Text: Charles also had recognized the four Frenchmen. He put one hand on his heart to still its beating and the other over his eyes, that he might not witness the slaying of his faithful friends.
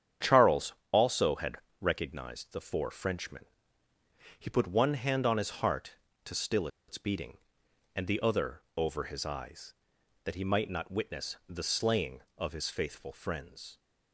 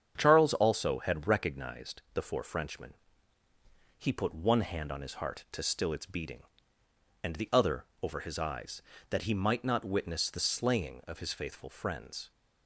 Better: second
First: starts louder than the rest; strong; until 1.4 s; 9 dB // pauses between "Charles" and "also"; slight; at 0.7 s; 0.20 s long // pauses between "had" and "recognized"; slight; at 1.5 s; 0.24 s long // pauses between "still" and "its"; slight; at 6.6 s; 0.20 s long // pauses between "other" and "over"; slight; at 8.6 s; 0.16 s long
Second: starts louder than the rest; strong; until 1.1 s; 7.5 dB // pauses between "other" and "over"; slight; at 7.8 s; 0.20 s long

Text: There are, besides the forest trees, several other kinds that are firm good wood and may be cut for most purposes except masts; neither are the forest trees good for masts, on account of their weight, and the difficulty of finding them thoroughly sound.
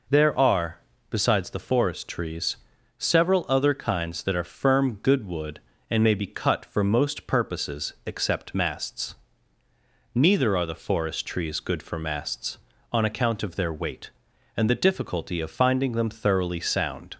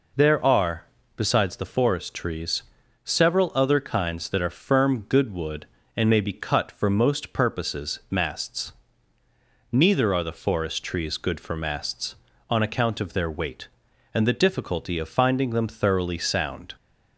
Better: first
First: none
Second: skips "except"; at 8.0 s

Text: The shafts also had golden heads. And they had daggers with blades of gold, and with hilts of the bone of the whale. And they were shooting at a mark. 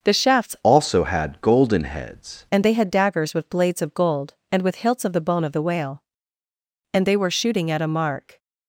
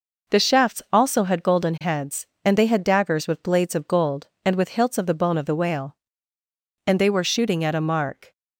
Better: second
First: starts louder than the rest; until 1.1 s; 6.5 dB // changes voice from "also" to "heads"; from 0.6 to 2.4 s; 1.8 s long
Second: none

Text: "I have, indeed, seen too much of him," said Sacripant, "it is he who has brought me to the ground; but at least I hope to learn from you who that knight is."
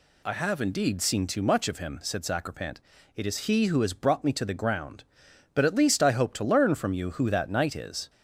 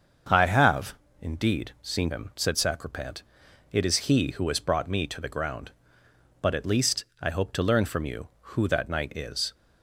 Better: first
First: none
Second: starts louder than the rest; until 1.5 s; 7 dB // skips "too much of"; at 2.1 s // pauses between "least" and "I"; slight; at 7.0 s; 0.18 s long

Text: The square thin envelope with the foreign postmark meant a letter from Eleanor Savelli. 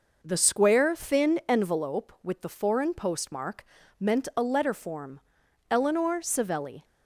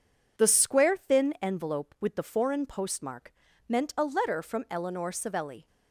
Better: second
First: pauses between "postmark" and "meant"; slight; at 3.6 s; 0.36 s long // says "form" for "from"; at 4.7 s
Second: pauses between "postmark" and "meant"; slight; at 3.3 s; 0.34 s long

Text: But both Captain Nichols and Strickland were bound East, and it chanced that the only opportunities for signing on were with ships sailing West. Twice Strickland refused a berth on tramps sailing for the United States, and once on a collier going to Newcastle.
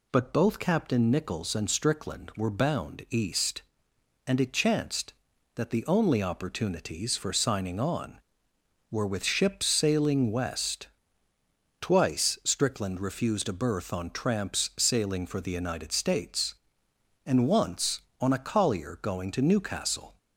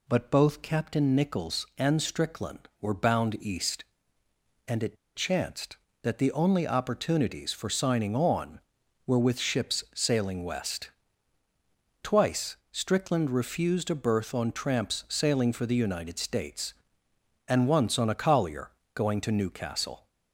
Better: first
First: none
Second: pauses between "it" and "chanced"; slight; at 4.9 s; 0.19 s long // pauses between "Twice" and "Strickland"; slight; at 12.5 s; 0.16 s long // pauses between "collier" and "going"; slight; at 18.7 s; 0.24 s long

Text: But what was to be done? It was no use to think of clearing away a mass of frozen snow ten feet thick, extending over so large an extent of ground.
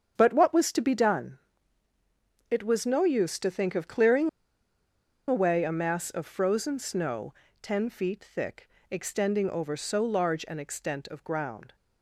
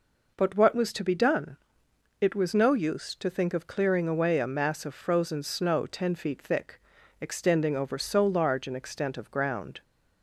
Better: second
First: starts louder than the rest; strong; until 1.1 s; 7.5 dB // pauses between "clearing" and "away"; at 4.2 s; 0.99 s long // pauses between "snow" and "ten"; slight; at 7.3 s; 0.28 s long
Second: none

